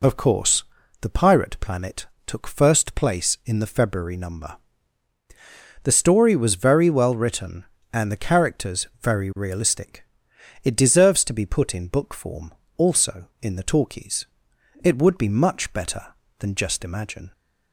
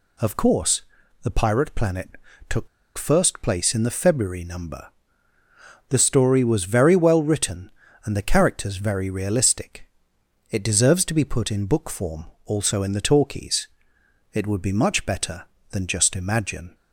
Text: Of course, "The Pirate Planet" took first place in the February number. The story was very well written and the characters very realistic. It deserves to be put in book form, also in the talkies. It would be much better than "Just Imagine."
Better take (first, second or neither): first